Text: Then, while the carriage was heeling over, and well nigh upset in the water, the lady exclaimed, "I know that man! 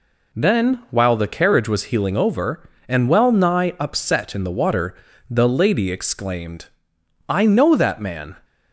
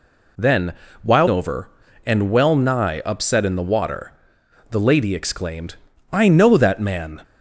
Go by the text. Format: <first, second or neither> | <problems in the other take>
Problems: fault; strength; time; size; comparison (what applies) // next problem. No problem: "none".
first | skips "the carriage was heeling"; at 1.2 s